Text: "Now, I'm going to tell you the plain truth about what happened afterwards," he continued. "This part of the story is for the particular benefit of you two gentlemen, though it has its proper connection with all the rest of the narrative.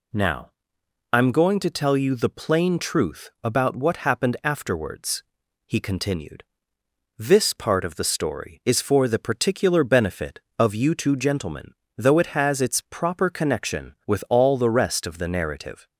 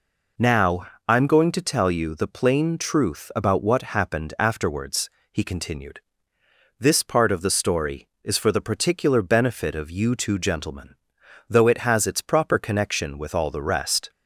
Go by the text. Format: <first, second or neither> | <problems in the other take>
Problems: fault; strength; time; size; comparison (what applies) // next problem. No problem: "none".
first | stops before "of the narrative"; at 14.0 s